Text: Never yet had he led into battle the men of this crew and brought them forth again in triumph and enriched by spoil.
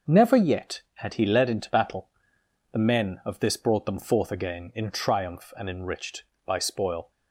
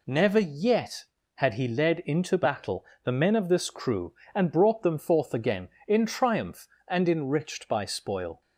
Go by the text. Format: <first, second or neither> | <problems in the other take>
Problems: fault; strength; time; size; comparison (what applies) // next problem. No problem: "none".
second | pauses between "battle" and "the"; noticeable; at 2.0 s; 0.62 s long; slight in the second // skips "crew and"; at 3.5 s